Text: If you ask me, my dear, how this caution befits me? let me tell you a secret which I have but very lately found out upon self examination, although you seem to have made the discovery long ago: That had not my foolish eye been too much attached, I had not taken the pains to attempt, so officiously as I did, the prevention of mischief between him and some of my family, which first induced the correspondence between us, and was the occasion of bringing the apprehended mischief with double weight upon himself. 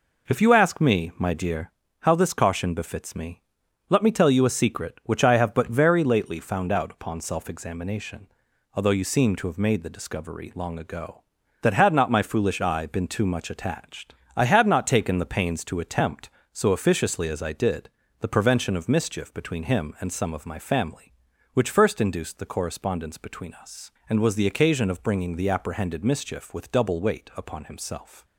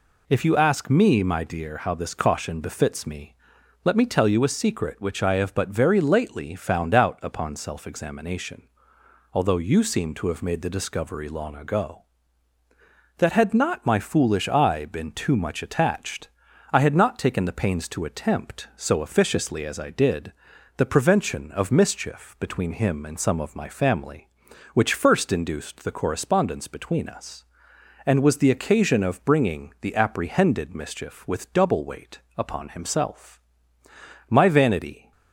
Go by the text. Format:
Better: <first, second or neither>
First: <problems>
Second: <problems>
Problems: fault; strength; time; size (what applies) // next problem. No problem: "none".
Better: first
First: none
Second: goes on to say "My vanity"; noticeable; from 34.2 s on; 0.84 s long